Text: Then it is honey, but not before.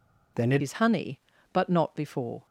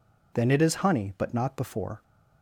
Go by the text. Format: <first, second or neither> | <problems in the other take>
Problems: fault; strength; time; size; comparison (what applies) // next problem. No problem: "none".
second | changes voice at "is"; from 0.5 s on; 1.9 s long